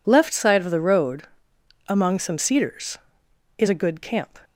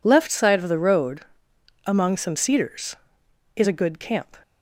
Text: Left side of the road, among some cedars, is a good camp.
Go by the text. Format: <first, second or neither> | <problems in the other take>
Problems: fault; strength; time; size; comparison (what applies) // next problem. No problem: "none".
neither | none